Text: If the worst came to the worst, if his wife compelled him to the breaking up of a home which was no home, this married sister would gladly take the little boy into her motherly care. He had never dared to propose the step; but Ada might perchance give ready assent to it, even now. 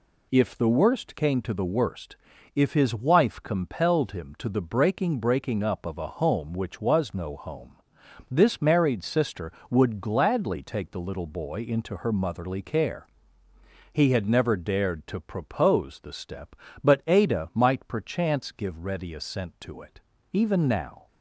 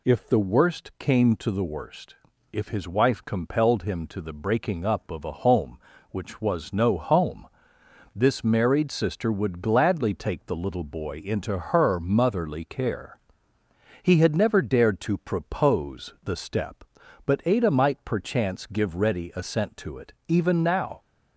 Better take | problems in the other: second | says "breaking" twice; at 5.1 s

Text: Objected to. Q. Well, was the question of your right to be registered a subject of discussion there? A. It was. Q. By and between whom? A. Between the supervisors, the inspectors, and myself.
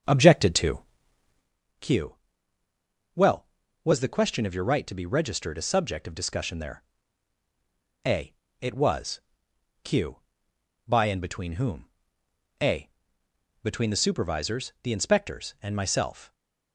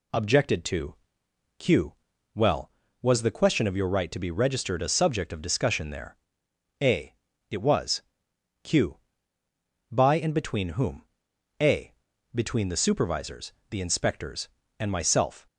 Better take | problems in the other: second | starts louder than the rest; until 1.6 s; 7 dB // stays silent after the last word; slight; from 16.2 s on; 0.5 s long

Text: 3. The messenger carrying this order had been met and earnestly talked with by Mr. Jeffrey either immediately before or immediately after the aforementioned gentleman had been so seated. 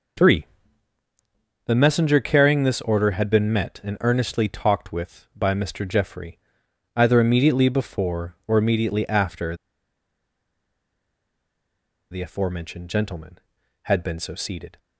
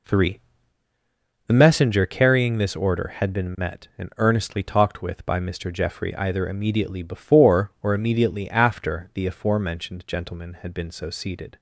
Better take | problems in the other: second | pauses between "Jeffrey" and "either"; noticeable; at 6.3 s; 0.56 s long // pauses between "after" and "the"; strong; at 9.5 s; 2.5 s long

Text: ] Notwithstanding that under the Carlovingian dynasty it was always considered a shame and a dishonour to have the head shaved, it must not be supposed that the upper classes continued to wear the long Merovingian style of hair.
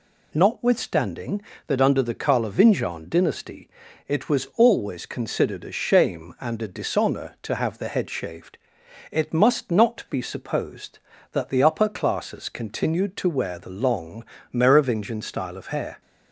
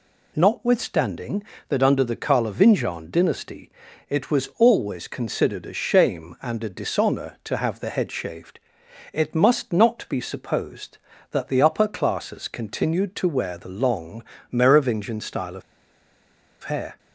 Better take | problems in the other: first | pauses between "dynasty" and "it"; at 3.7 s; 0.38 s long; also in the first // pauses between "long" and "Merovingian"; slight; at 14.2 s; 0.28 s long; slight in the first // pauses between "of" and "hair"; at 15.6 s; 1.0 s long

